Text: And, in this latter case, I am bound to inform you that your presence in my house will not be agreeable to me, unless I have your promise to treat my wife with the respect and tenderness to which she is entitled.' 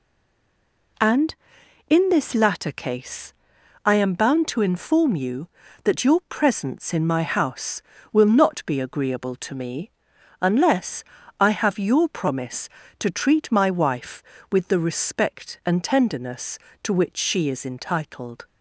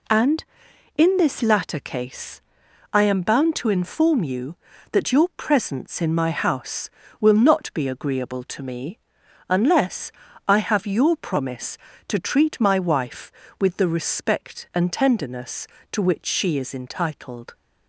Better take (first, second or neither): second